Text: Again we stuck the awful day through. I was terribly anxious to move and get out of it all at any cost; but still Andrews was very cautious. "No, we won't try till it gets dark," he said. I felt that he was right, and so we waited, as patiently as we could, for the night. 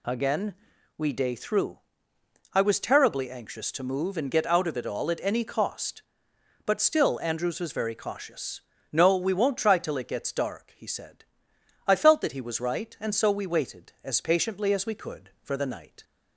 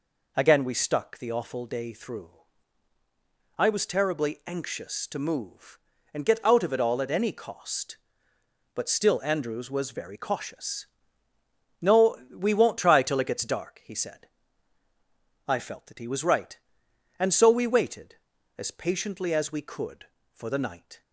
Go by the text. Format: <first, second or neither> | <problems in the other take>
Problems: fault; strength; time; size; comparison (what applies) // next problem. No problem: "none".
second | pauses between "Again" and "we"; at 0.5 s; 0.44 s long // skips "stuck the awful"; at 1.1 s